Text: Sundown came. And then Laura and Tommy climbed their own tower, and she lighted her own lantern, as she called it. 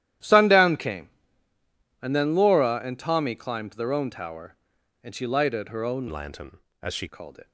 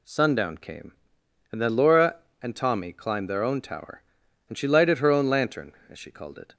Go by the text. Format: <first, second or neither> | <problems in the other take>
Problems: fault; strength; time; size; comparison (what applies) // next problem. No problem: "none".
second | starts louder than the rest; strong; until 2.1 s; 12 dB // changes voice from "lantern" to "she"; from 6.0 to 7.0 s; 1.0 s long